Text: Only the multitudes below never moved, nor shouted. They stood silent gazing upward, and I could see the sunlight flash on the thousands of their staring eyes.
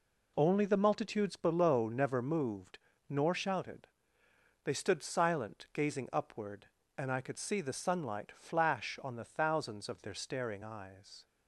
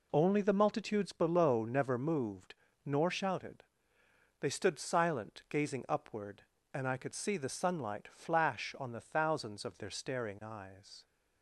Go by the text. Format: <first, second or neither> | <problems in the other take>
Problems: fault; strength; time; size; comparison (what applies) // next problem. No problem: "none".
neither | none